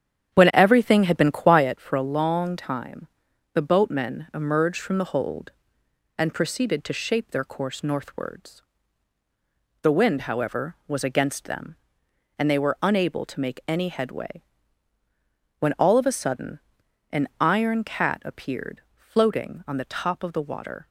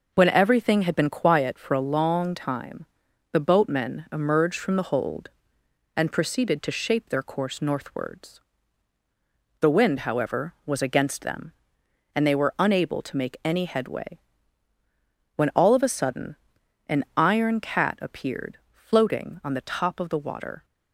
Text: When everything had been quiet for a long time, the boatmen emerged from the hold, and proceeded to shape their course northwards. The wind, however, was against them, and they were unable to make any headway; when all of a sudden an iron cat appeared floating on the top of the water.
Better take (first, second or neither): second